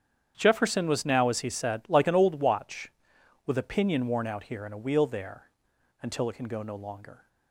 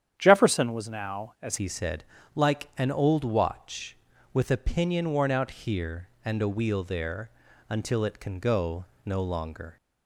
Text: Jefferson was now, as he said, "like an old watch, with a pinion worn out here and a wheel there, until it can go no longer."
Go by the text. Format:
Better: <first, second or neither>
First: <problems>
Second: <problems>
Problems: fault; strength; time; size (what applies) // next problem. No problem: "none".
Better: first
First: starts louder than the rest; strong; until 1.3 s; 9 dB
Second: starts louder than the rest; strong; until 1.1 s; 9.5 dB // changes voice at "he"; from 1.5 s on; 8.2 s long // pauses between "go" and "no"; slight; at 8.8 s; 0.18 s long